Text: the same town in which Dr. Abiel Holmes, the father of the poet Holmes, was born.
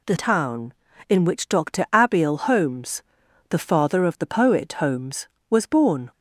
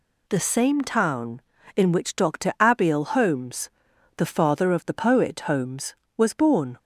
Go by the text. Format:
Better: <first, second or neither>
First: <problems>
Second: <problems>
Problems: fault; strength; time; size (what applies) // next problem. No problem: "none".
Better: second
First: skips "same"; at 0.1 s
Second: none